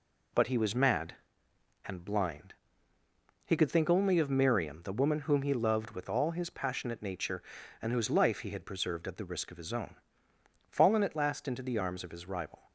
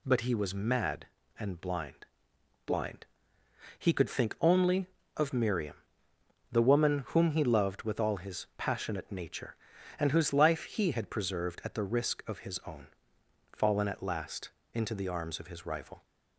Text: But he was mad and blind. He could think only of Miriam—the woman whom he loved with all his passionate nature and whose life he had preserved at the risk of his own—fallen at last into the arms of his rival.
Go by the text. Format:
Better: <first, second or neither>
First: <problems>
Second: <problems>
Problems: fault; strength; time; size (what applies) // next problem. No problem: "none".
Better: first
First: none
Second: says "blind" twice; at 2.6 s // pauses between "last" and "into"; slight; at 14.4 s; 0.24 s long